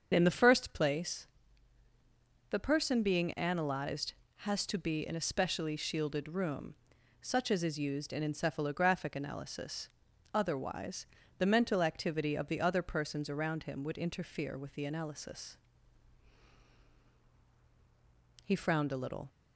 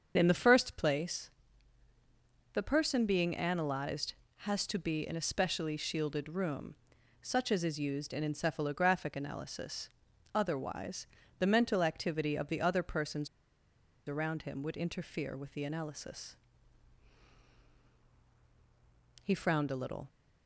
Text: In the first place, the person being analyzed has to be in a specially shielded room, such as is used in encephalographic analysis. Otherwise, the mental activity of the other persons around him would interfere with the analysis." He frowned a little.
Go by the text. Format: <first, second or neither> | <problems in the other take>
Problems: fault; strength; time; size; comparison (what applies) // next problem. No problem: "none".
first | starts louder than the rest; until 1.1 s; 7 dB; also in the first // pauses between "persons" and "around"; noticeable; at 13.2 s; 0.78 s long